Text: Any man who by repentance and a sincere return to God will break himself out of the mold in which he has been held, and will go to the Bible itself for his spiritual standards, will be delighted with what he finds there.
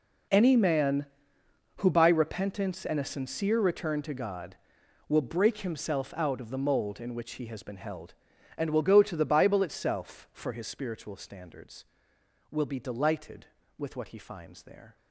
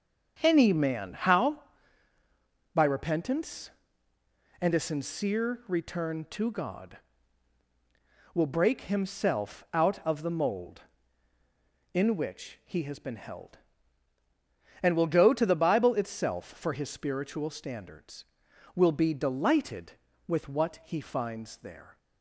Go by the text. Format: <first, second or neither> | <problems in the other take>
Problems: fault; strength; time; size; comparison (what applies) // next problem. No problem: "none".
first | starts louder than the rest; strong; until 1.4 s; 7 dB // says "how" for "who"; at 1.1 s